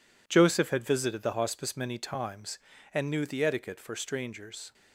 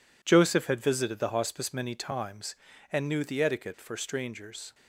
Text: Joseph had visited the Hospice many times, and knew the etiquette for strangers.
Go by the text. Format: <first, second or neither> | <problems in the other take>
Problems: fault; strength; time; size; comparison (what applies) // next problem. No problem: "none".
neither | none